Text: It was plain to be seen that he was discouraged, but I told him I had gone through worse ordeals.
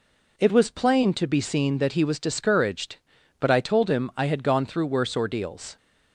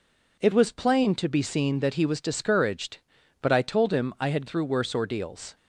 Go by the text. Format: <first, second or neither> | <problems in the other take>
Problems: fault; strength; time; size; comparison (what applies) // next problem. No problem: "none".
first | skips "gone"; at 4.4 s